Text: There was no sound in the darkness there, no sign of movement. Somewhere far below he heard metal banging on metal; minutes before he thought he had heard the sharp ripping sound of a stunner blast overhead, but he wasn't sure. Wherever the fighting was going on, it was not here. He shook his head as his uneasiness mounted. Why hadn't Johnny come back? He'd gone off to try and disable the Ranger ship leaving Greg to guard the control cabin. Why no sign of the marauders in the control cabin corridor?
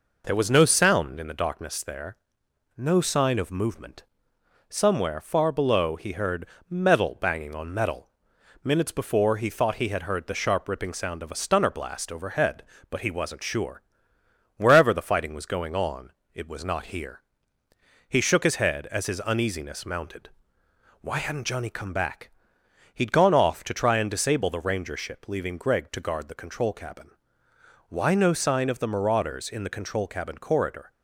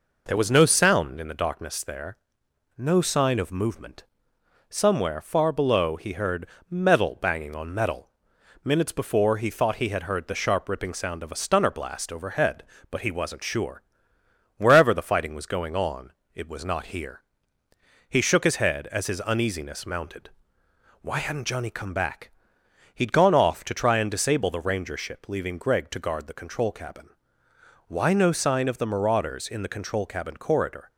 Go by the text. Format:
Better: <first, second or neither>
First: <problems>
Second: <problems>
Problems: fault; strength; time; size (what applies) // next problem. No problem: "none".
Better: neither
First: pauses between "heard" and "metal"; slight; at 6.4 s; 0.20 s long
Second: pauses between "heard" and "metal"; slight; at 6.4 s; 0.20 s long